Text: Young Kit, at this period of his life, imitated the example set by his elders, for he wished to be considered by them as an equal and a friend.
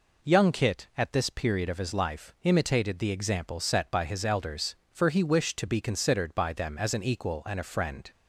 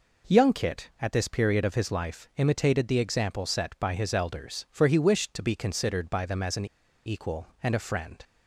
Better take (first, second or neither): first